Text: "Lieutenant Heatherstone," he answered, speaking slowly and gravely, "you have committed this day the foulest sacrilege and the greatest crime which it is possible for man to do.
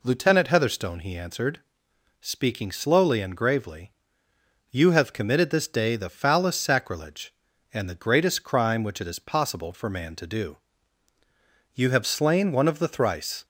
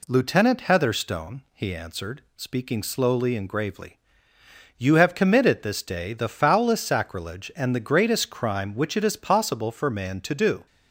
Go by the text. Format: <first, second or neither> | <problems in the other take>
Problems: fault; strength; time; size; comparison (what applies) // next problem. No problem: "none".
second | goes on to say "You have slain one of the thrice"; strong; from 11.7 s on; 1.7 s long